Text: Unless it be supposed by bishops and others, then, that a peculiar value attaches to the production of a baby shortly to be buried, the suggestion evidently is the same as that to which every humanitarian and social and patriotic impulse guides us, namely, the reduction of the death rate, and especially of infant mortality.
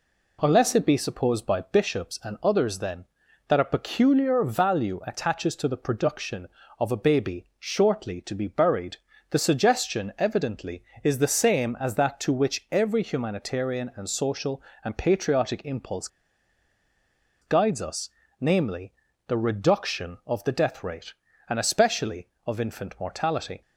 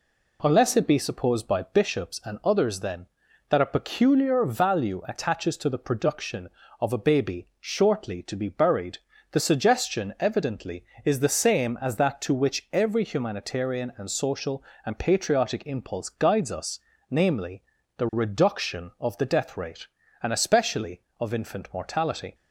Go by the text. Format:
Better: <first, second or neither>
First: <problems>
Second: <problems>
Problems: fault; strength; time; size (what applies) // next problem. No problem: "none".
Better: second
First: pauses between "impulse" and "guides"; strong; at 16.0 s; 1.3 s long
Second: none